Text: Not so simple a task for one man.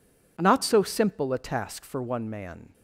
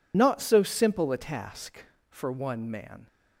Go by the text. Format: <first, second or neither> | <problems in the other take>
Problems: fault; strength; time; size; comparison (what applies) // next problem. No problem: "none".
first | loses the start of "Not"; at 0.1 s; 40 ms